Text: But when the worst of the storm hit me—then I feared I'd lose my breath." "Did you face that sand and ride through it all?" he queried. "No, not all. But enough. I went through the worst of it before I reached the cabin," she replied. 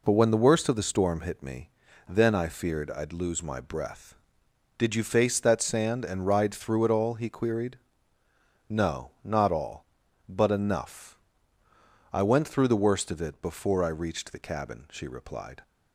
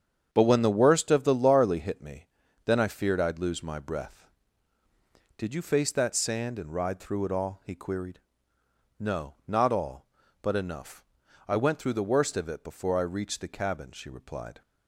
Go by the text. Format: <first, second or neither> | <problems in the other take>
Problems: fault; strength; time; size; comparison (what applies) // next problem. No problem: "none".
first | starts louder than the rest; strong; until 1.3 s; 8 dB // says "larly" for "storm"; at 1.3 s